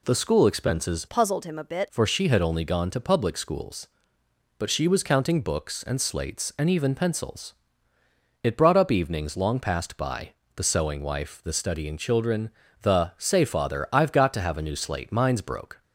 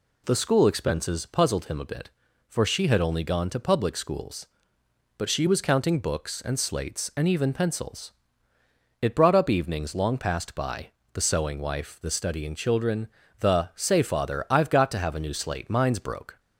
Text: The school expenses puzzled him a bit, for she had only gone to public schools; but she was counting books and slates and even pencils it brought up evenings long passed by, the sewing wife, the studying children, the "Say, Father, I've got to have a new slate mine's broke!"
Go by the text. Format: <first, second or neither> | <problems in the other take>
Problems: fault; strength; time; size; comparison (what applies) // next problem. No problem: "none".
second | changes voice from "puzzled" to "bit"; from 1.0 to 1.8 s; 0.8 s long // pauses between "pencils" and "it"; noticeable; at 7.5 s; 0.88 s long; noticeable in the second